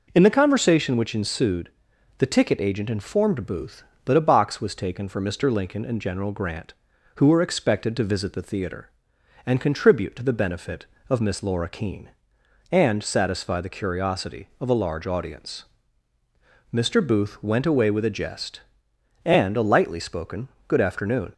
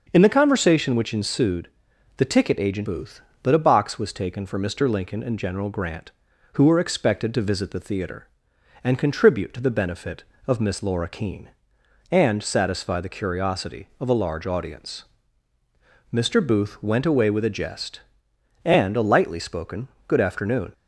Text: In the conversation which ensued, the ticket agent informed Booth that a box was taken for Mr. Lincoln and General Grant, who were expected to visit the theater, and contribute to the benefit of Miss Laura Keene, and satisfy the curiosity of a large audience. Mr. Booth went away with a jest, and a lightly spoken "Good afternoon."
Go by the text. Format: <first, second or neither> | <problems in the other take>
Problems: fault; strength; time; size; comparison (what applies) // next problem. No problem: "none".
first | starts louder than the rest; noticeable; until 1.1 s; 6 dB // skips "informed"; at 2.8 s // pauses between "spoken" and "Good"; slight; at 19.8 s; 0.22 s long; slight in the first